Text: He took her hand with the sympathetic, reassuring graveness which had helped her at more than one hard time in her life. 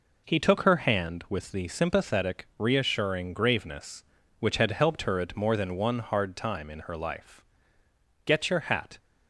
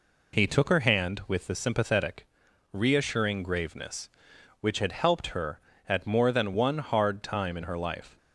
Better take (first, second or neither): second